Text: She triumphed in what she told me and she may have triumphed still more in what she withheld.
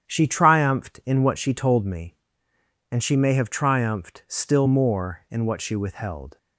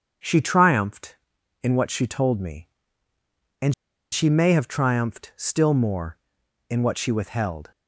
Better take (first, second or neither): first